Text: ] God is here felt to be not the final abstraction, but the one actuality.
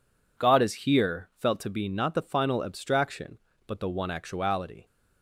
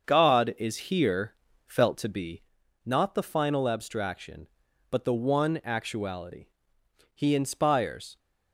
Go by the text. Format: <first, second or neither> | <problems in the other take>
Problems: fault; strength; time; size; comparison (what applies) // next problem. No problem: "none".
first | starts louder than the rest; until 1.0 s; 6.5 dB // pauses between "here" and "felt"; slight; at 1.3 s; 0.34 s long // pauses between "be" and "not"; at 2.4 s; 0.42 s long // goes on to say "He inspires"; noticeable; from 7.1 s on; 1.0 s long